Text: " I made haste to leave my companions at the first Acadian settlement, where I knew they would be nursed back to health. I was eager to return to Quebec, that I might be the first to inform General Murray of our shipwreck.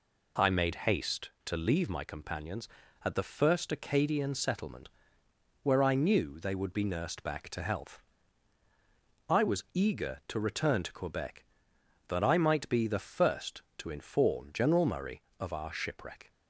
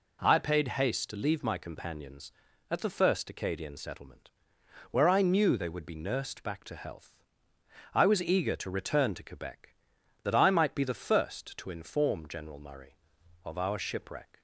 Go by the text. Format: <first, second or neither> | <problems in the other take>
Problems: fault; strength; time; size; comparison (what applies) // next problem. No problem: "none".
first | says "paid" for "made"; at 0.3 s